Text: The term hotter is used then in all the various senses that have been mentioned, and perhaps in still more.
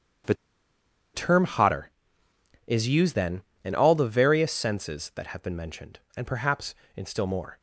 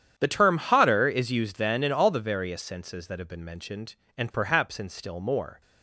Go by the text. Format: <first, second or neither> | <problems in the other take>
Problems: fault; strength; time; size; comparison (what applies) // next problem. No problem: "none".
second | starts louder than the rest; strong; until 2.8 s; 8.5 dB; strong in the second // pauses between "The" and "term"; noticeable; at 0.3 s; 0.80 s long